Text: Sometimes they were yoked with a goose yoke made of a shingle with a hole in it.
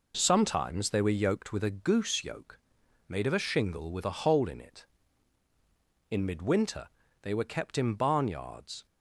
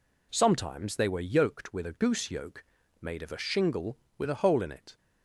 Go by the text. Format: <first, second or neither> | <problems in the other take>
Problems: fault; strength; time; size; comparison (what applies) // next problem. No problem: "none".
second | pauses between "yoke" and "made"; noticeable; at 2.5 s; 0.48 s long; slight in the second // goes on to say "In midwinter they were kept in barnyards"; strong; from 6.0 s on; 2.7 s long